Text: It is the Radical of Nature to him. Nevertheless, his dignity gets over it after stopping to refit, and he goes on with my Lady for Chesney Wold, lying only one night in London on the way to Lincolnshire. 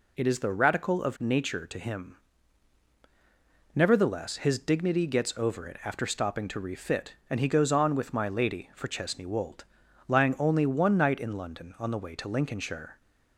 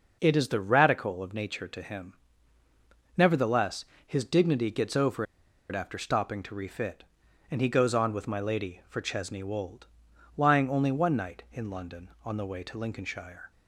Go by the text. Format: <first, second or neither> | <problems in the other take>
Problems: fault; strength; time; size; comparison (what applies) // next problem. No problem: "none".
first | pauses between "over" and "it"; noticeable; at 5.2 s; 0.46 s long